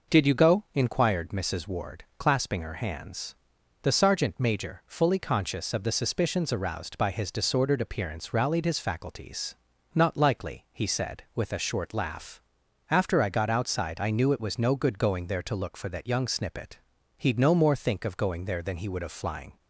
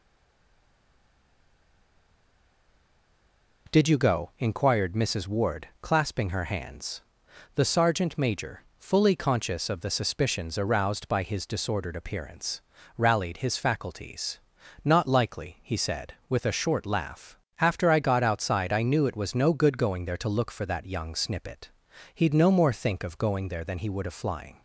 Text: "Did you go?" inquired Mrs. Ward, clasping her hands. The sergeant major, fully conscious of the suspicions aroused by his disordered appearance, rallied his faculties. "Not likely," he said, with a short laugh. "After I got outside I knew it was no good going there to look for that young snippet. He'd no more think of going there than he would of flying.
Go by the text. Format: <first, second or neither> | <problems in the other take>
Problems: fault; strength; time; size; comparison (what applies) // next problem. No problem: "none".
first | stays silent before the first word; strong; until 3.6 s; 3.6 s long